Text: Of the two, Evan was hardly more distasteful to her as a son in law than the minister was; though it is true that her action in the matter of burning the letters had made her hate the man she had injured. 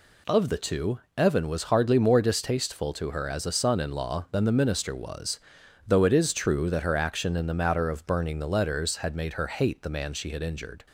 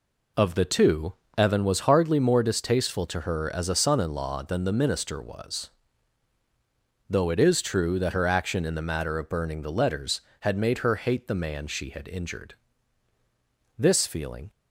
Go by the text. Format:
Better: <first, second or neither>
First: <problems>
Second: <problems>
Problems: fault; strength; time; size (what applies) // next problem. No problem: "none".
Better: first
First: none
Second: goes on to say "This feeling"; noticeable; from 13.7 s on; 0.72 s long